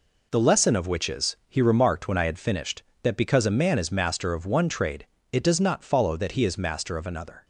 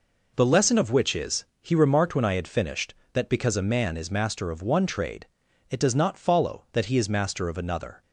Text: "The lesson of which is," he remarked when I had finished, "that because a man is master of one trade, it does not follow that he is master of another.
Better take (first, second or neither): neither